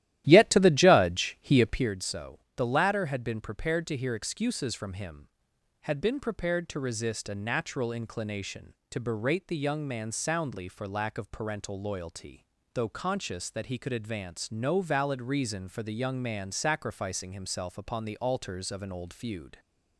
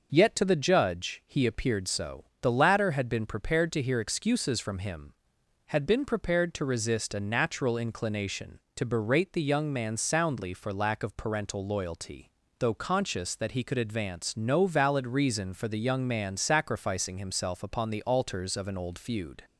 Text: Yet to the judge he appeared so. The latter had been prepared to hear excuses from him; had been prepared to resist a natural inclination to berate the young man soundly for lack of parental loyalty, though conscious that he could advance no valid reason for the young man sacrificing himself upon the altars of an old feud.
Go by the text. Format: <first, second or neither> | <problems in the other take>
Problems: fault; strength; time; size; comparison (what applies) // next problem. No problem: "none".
second | starts louder than the rest; strong; until 1.9 s; 13.5 dB